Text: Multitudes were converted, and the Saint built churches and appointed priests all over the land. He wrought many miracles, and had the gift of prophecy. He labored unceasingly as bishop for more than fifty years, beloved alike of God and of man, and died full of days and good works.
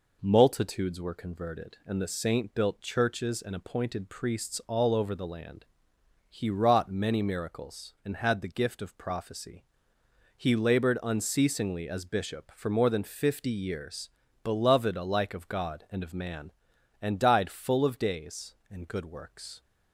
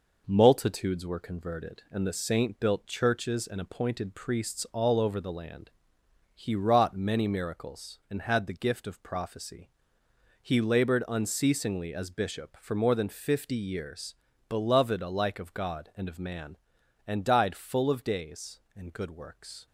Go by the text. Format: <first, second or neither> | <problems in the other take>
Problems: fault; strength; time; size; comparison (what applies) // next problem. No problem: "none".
first | gets quieter; throughout; 3.5 dB